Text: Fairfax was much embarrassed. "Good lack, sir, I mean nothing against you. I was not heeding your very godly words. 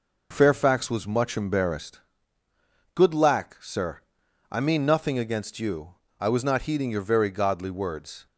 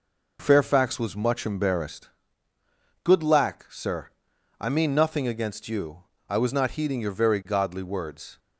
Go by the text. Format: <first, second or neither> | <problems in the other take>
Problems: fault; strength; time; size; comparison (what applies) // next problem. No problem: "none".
neither | none